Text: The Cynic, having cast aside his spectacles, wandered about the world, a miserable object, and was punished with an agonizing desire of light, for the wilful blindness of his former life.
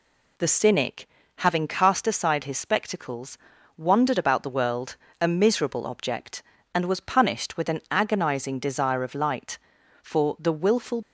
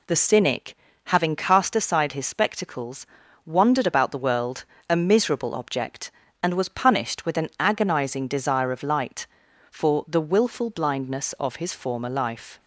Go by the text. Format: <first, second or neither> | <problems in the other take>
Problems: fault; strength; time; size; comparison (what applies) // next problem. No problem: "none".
second | stops before "blindness of his former life"; at 11.0 s